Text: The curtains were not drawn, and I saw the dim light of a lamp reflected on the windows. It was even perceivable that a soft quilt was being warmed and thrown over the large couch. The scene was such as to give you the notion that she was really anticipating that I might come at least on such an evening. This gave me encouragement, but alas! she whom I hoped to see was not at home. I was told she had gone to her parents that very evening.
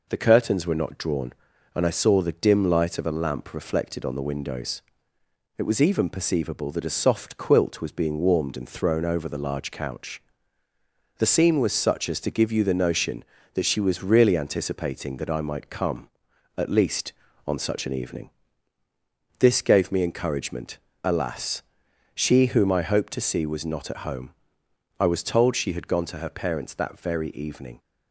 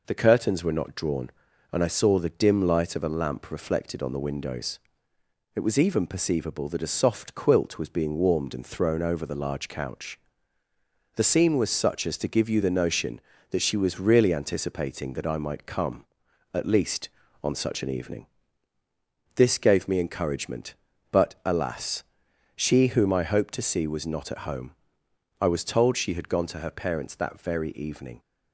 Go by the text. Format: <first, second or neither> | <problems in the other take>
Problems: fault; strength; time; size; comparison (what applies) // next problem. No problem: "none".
second | skips "but"; at 20.9 s